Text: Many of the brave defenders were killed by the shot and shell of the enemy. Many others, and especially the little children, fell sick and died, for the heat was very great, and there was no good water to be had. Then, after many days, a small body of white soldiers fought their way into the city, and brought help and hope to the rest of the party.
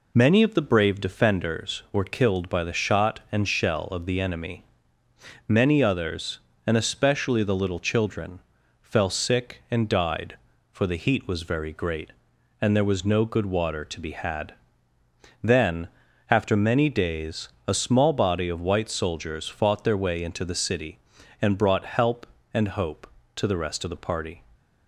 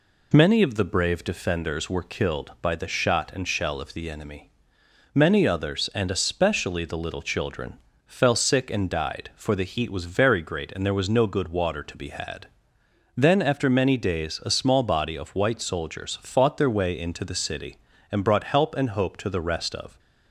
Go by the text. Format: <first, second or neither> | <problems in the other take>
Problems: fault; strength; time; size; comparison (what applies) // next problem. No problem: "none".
first | stops before "the party"; at 19.9 s